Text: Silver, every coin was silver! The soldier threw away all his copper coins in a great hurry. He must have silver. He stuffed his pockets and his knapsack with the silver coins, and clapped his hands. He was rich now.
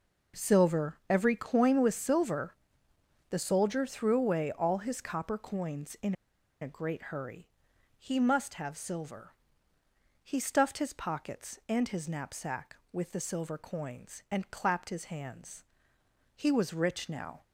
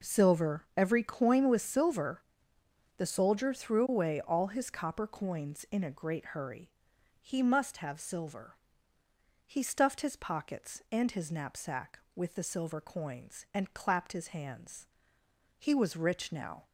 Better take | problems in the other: second | pauses between "in" and "a"; noticeable; at 6.1 s; 0.48 s long

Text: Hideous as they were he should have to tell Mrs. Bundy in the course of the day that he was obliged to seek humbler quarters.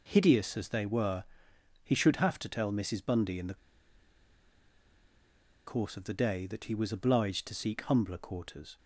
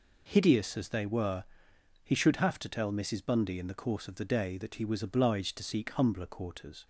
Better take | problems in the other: second | pauses between "were" and "he"; noticeable; at 1.2 s; 0.58 s long; noticeable in the second // pauses between "the" and "course"; strong; at 3.5 s; 2.1 s long

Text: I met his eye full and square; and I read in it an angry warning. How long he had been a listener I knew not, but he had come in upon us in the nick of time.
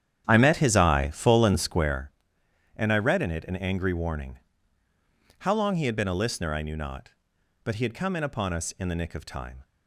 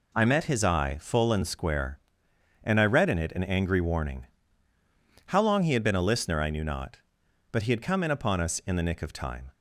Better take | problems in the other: second | starts louder than the rest; strong; until 2.0 s; 9.5 dB

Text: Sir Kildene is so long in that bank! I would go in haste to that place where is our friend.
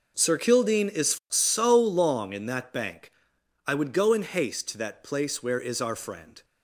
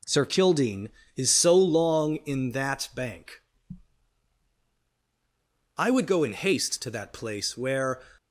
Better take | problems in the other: first | stops before "is our friend"; at 8.1 s

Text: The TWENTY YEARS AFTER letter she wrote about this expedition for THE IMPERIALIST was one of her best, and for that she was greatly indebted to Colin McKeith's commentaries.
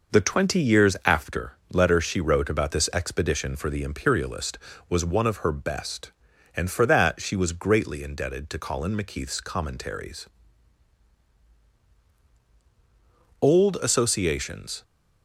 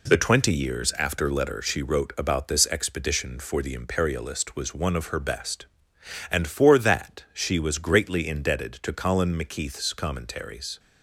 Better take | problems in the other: second | pauses between "AFTER" and "letter"; slight; at 1.5 s; 0.16 s long // goes on to say "Old associations"; from 13.3 s on; 1.4 s long

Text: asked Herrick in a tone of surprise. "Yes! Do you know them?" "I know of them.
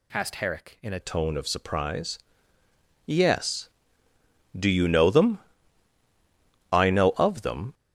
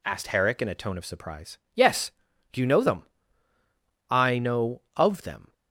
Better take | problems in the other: second | changes voice at "tone"; from 0.9 s on; 6.8 s long

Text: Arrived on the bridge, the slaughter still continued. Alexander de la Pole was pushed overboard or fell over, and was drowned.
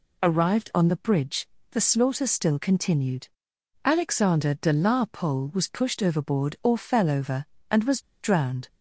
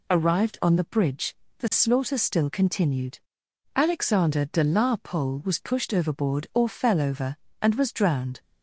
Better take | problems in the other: second | pauses between "was" and "drowned"; slight; at 8.0 s; 0.19 s long

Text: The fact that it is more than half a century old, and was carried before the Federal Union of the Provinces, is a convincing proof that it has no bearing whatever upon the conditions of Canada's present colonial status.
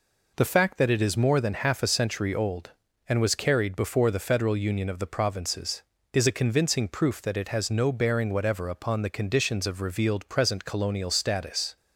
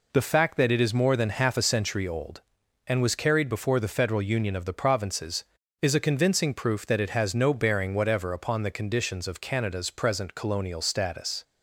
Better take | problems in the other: second | says "Revealed" for "Canada's"; at 9.8 s

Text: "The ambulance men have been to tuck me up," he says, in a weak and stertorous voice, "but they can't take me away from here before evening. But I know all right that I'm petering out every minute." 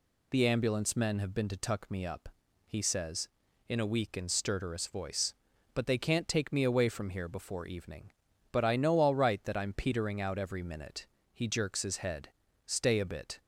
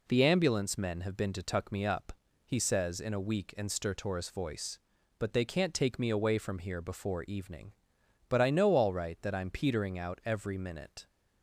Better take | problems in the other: second | goes on to say "He jerks his head Stay a bit"; strong; from 11.3 s on; 2.0 s long

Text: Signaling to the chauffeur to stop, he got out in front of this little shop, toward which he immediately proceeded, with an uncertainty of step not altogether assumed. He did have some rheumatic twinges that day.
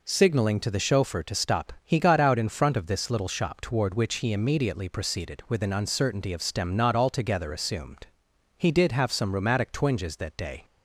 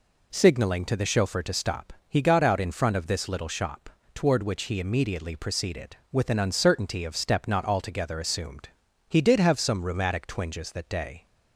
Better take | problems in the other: second | says "stem" for "step"; at 6.4 s

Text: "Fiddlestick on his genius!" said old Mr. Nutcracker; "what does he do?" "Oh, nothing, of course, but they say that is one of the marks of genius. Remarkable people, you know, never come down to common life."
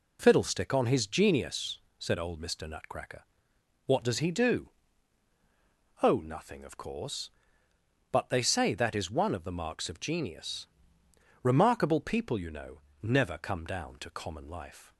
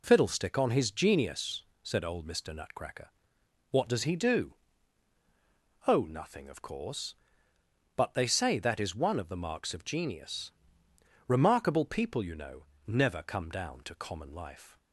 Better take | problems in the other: neither | none

